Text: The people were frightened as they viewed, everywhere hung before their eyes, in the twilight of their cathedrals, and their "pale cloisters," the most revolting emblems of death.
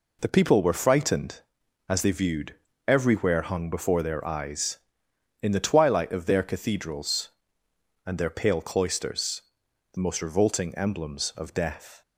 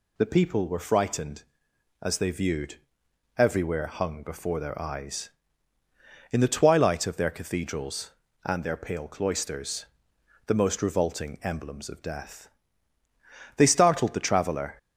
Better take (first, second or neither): first